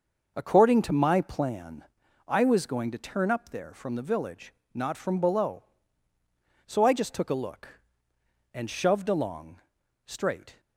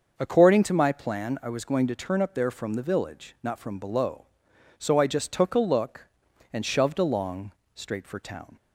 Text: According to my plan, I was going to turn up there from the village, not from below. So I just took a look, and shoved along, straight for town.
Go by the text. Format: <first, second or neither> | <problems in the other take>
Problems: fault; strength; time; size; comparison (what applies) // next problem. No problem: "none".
second | starts louder than the rest; noticeable; until 1.3 s; 6 dB; also in the second // stops before "for town"; at 10.5 s